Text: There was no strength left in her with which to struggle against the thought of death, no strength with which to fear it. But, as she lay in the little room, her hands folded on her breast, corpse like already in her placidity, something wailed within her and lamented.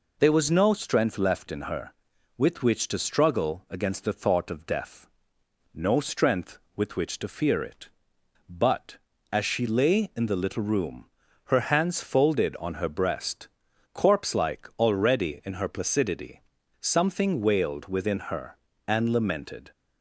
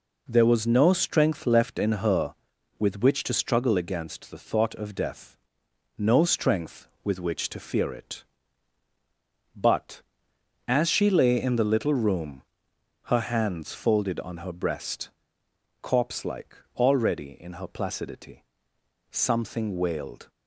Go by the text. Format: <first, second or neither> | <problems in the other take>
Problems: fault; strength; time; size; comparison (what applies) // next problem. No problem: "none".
first | pauses between "like" and "already"; slight; at 16.5 s; 0.20 s long // stops before "within her and lamented"; at 20.2 s